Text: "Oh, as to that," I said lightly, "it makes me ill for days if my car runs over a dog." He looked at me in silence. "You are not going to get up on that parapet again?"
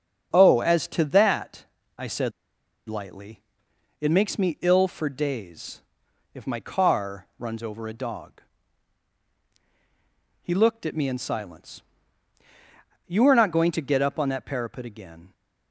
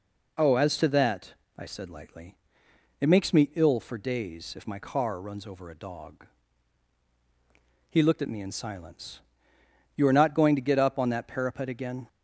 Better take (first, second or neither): second